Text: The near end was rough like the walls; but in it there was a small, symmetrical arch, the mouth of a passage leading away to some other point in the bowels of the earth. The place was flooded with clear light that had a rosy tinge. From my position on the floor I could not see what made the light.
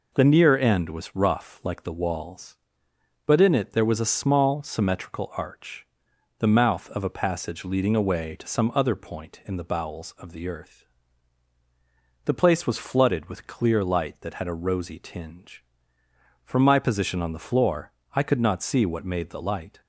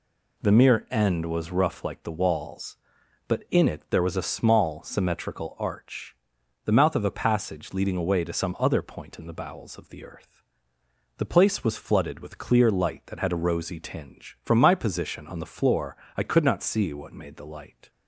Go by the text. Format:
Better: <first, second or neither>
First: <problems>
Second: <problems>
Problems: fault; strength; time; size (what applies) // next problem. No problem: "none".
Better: first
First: pauses between "floor" and "I"; slight; at 17.9 s; 0.22 s long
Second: says "mere" for "near"; at 0.5 s // pauses between "floor" and "I"; slight; at 15.9 s; 0.20 s long